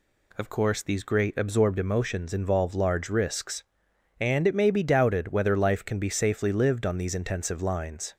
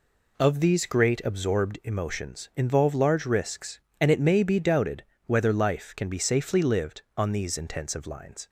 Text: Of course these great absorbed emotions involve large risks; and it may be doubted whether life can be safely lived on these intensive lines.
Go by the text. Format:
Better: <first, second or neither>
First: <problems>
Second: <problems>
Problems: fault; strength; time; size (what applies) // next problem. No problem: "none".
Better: first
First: none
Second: skips "course"; at 0.5 s // pauses between "doubted" and "whether"; slight; at 5.0 s; 0.22 s long